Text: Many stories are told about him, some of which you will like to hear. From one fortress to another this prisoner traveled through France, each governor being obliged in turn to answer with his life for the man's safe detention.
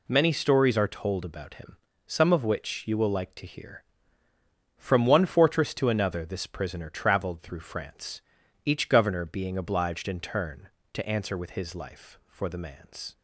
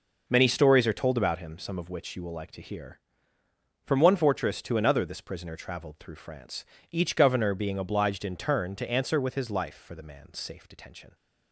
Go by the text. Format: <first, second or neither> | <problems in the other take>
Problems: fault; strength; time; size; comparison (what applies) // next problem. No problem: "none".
second | stops before "safe detention"; at 13.1 s